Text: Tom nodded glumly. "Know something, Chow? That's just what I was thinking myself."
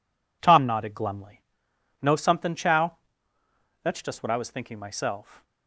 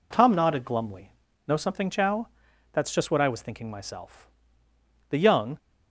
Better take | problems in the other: first | goes on to say "The young"; from 5.0 s on; 0.50 s long

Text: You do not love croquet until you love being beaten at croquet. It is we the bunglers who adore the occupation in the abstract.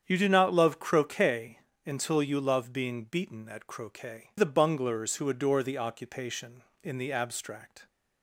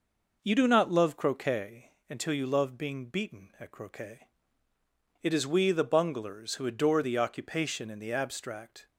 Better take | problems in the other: second | starts louder than the rest; strong; until 1.0 s; 8 dB // pauses between "croquet" and "until"; slight; at 1.5 s; 0.26 s long; slight in the second // skips "It is we"; at 4.3 s

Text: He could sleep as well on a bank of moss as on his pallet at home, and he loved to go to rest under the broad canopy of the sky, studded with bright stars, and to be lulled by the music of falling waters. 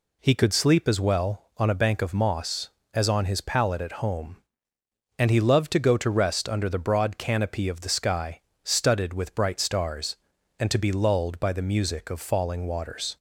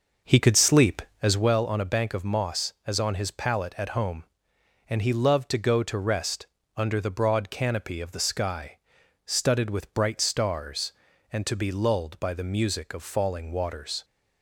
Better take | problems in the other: first | starts louder than the rest; noticeable; until 1.5 s; 6 dB // pauses between "rest" and "under"; slight; at 6.4 s; 0.30 s long

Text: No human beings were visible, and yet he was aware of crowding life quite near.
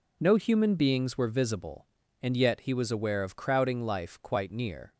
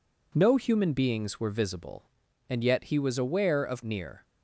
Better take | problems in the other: first | skips "crowding life quite"; at 3.8 s

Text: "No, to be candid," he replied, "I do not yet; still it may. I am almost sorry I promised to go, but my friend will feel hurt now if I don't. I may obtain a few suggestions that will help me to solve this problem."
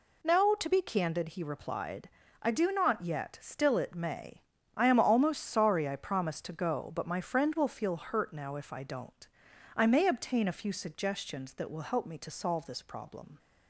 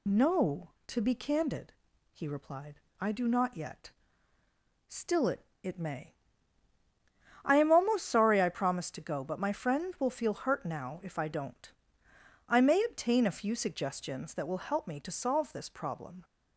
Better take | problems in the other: first | says "it" twice; at 5.6 s

